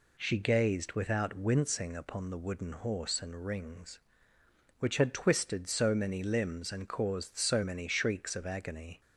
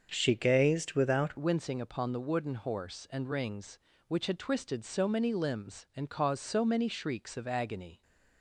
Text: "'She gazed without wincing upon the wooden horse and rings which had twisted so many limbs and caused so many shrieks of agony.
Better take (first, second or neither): first